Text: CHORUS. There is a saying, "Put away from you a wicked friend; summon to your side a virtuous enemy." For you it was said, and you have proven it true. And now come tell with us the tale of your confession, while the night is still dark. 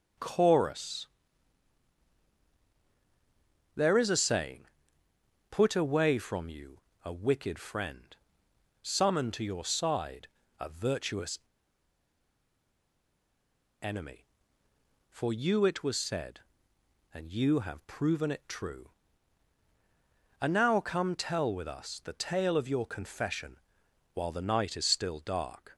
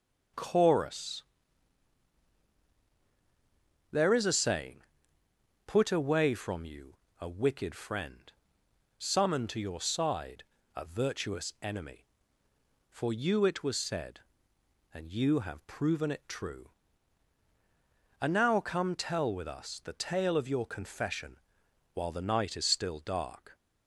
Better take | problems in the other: second | pauses between "you" and "a"; slight; at 6.7 s; 0.24 s long; slight in the second // pauses between "side" and "a"; slight; at 10.2 s; 0.30 s long; slight in the second // pauses between "virtuous" and "enemy"; strong; at 11.3 s; 2.4 s long

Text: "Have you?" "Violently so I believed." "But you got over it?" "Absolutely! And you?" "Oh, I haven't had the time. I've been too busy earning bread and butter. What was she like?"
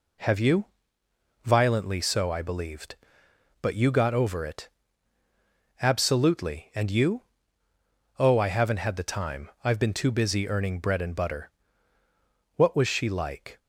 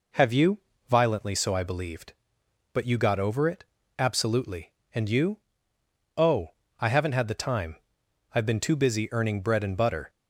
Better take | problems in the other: first | stops before "What was she like"; at 10.0 s

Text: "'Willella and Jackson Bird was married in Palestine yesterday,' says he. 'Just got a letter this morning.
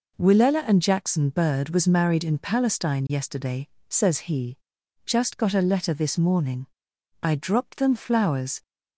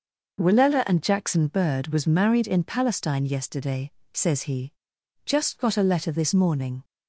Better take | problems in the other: second | goes on to say "I dropped them flowers"; from 7.2 s on; 1.4 s long

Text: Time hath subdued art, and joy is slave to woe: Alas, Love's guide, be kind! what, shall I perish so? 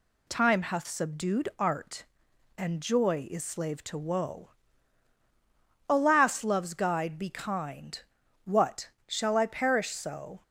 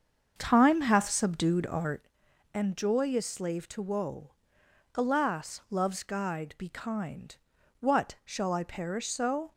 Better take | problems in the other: first | starts louder than the rest; until 2.1 s; 7 dB

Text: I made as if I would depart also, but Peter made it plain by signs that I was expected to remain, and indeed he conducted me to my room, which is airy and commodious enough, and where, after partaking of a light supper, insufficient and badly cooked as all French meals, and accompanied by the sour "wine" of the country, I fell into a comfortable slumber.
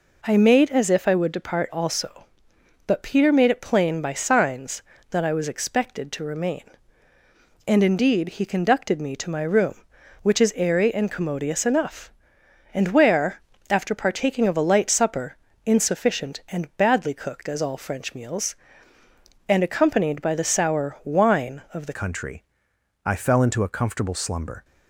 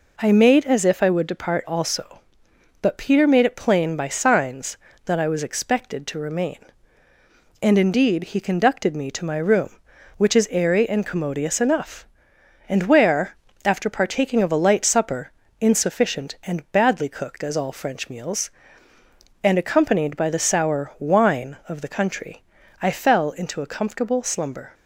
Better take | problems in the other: second | changes voice at "country"; from 21.9 s on; 2.7 s long

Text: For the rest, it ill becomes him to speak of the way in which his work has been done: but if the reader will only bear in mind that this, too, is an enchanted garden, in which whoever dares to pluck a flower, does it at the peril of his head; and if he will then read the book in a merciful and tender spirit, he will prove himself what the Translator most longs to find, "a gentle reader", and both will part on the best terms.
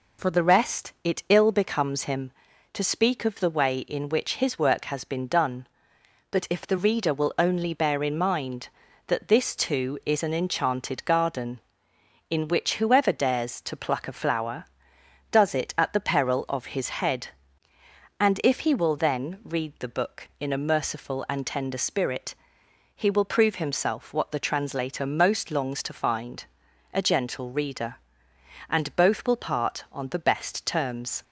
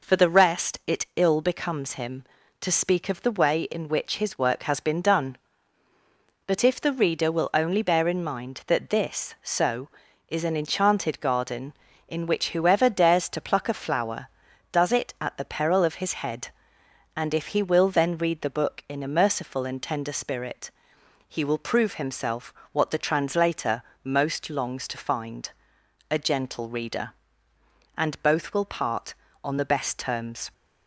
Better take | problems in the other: first | says "so" for "too"; at 9.4 s // pauses between "himself" and "what"; slight; at 22.5 s; 0.20 s long // pauses between "Translator" and "most"; slight; at 23.8 s; 0.22 s long

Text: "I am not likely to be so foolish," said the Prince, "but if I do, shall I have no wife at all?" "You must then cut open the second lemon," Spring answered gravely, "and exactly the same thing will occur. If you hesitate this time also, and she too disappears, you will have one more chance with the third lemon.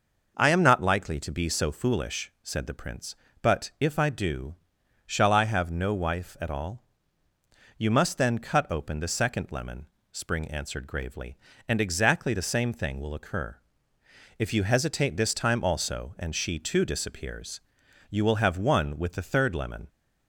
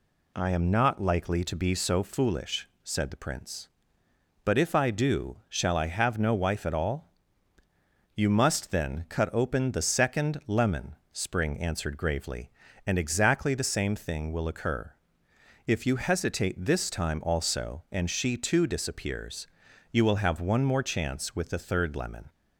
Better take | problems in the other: second | skips "more chance"; at 18.9 s

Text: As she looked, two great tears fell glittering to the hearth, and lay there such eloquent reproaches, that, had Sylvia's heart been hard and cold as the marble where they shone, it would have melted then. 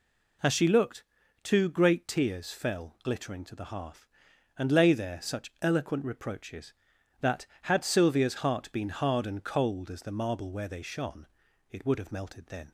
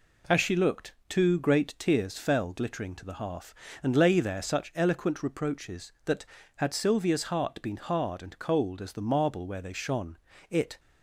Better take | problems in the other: first | stops before "would have melted then"; at 10.7 s

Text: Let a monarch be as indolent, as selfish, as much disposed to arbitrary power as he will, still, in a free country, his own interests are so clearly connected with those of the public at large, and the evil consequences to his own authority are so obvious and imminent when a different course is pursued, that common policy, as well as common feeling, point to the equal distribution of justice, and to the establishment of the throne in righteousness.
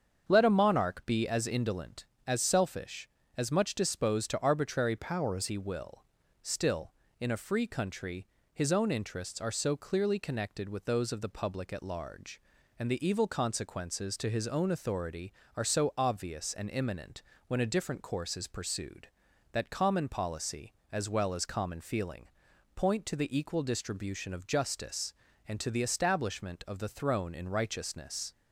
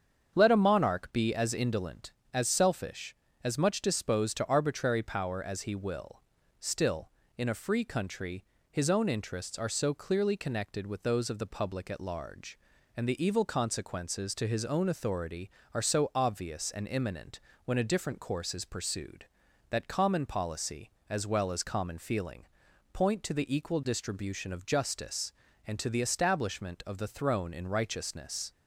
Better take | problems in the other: second | starts louder than the rest; strong; until 1.2 s; 7 dB; strong in the second // changes voice from "power" to "as"; from 4.9 to 5.4 s; 0.5 s long // pauses between "imminent" and "when"; slight; at 17.2 s; 0.26 s long; slight in the second

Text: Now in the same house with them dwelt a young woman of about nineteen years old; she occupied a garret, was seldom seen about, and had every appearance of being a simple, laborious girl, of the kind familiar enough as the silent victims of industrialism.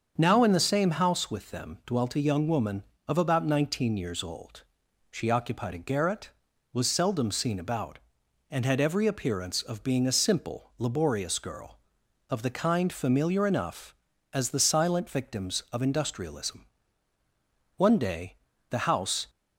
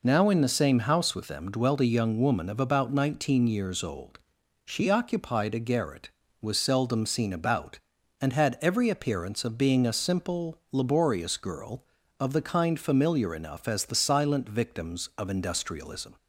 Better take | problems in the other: second | starts louder than the rest; until 1.1 s; 7 dB // goes on to say "One day the house"; from 17.7 s on; 1.5 s long

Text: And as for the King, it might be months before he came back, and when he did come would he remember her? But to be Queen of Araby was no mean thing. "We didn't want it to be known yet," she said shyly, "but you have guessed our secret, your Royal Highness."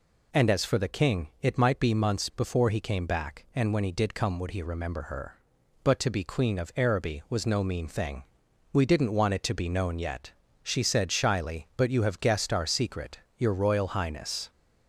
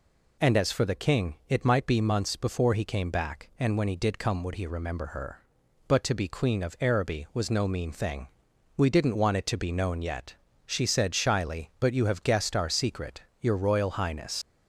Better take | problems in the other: first | leaves "Highness" unfinished; at 14.4 s; 110 ms

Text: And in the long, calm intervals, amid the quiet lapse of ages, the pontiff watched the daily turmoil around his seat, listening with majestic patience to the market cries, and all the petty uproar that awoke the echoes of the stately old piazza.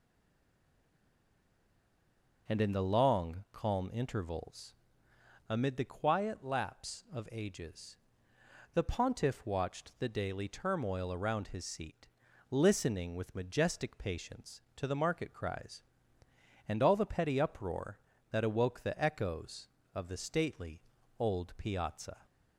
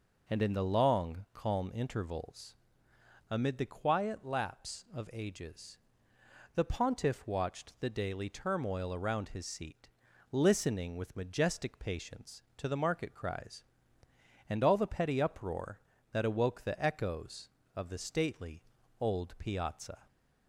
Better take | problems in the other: second | stays silent before the first word; until 2.4 s; 2.4 s long // pauses between "stately" and "old"; slight; at 20.8 s; 0.36 s long; slight in the second

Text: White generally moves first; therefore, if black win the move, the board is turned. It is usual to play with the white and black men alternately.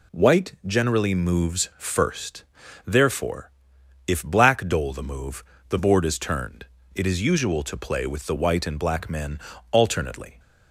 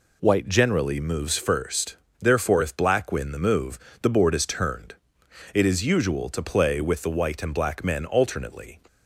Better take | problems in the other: second | says "dole" for "win"; at 4.6 s // pauses between "men" and "alternately"; slight; at 9.3 s; 0.36 s long

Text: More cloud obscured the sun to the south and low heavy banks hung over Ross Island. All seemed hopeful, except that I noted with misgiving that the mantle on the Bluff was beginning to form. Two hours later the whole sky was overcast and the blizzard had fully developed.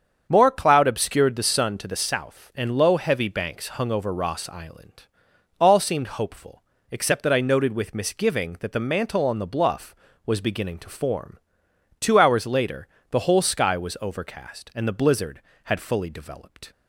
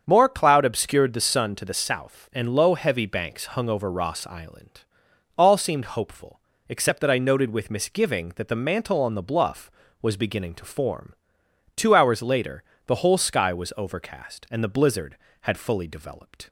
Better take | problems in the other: neither | starts louder than the rest; strong; the same in both // pauses between "later" and "the"; slight; the same in both

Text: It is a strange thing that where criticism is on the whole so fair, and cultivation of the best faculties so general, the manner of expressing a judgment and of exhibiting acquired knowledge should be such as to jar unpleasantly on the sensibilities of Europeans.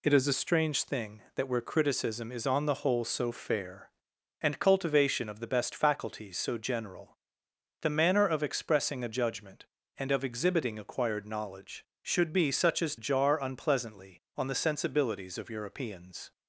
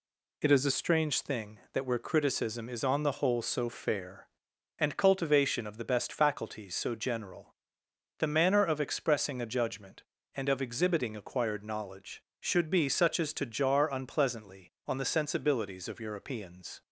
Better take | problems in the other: second | skips "to"; at 12.9 s

